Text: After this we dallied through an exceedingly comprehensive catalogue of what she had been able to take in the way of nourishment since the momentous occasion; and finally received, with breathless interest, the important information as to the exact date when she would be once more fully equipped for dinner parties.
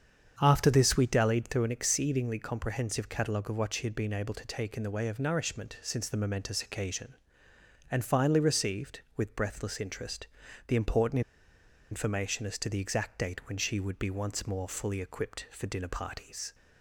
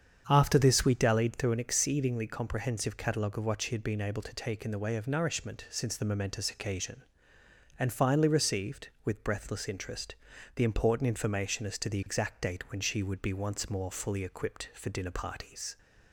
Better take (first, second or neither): second